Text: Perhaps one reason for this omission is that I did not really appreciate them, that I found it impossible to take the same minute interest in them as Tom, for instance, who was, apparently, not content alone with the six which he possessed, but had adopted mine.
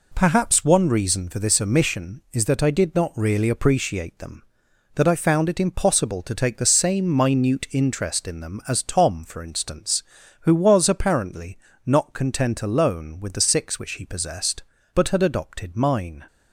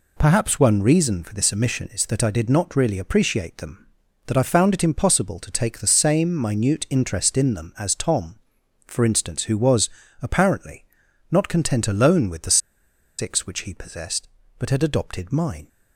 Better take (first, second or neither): first